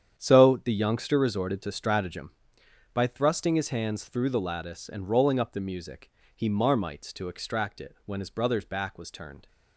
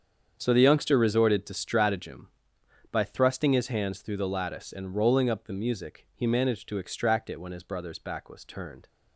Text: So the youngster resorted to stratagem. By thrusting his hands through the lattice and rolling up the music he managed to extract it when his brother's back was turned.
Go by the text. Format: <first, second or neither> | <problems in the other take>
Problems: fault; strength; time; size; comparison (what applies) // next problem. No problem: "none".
second | starts louder than the rest; strong; until 1.2 s; 8.5 dB; strong in the second // pauses between "music" and "he"; slight; at 6.0 s; 0.28 s long // says "marmites" for "managed"; at 6.4 s